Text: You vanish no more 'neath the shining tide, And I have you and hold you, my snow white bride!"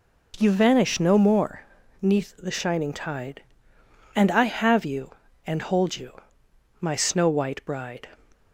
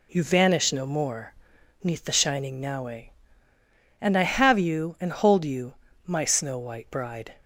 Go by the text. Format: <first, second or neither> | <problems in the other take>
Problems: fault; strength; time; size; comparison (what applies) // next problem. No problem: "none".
first | pauses between "more" and "neath"; noticeable; at 1.3 s; 0.48 s long; also in the first // says "naue" for "tide"; at 2.5 s